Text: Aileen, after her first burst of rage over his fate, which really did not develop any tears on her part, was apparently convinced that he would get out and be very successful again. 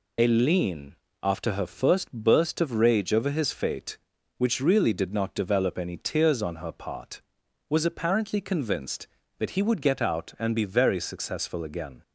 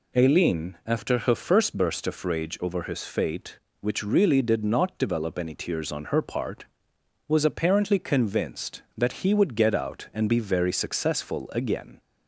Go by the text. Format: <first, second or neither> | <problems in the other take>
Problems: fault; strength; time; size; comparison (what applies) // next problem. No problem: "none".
second | loses the start of "Aileen"; at 0.1 s; 35 ms